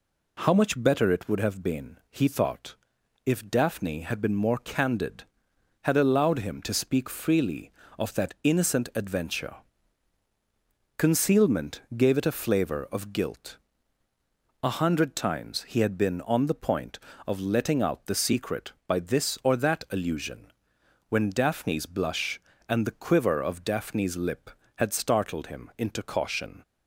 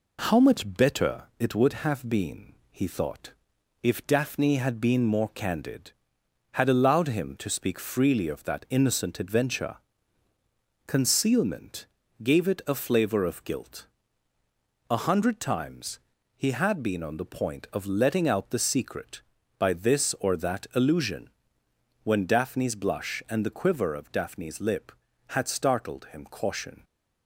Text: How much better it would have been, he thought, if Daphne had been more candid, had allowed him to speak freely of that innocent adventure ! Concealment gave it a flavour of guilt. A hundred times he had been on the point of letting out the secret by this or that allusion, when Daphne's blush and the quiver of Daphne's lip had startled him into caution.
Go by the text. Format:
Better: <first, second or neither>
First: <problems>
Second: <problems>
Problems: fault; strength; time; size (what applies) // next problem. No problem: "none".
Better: first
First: pauses between "Concealment" and "gave"; slight; at 11.8 s; 0.16 s long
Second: pauses between "better" and "it"; slight; at 1.2 s; 0.16 s long // pauses between "Concealment" and "gave"; slight; at 11.8 s; 0.36 s long // pauses between "times" and "he"; slight; at 15.9 s; 0.36 s long // skips "into"; at 26.2 s